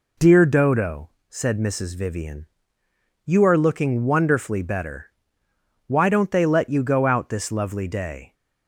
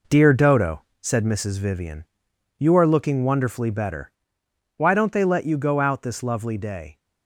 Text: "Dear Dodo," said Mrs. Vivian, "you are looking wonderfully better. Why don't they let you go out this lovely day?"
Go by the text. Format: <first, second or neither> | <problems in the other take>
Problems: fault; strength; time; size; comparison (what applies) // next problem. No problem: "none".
first | gets quieter; strong; throughout; 7.5 dB